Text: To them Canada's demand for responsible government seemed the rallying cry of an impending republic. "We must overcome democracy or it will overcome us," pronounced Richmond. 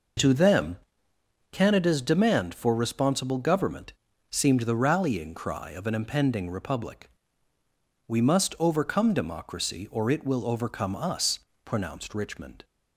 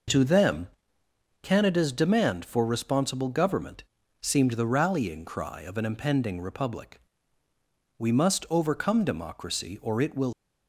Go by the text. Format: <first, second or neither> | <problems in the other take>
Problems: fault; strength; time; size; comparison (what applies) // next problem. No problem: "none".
first | pauses between "them" and "Canada's"; noticeable; at 0.6 s; 0.74 s long; noticeable in the first // pauses between "government" and "seemed"; at 3.8 s; 0.40 s long; also in the first // stops before "overcome us pronounced Richmond"; at 10.3 s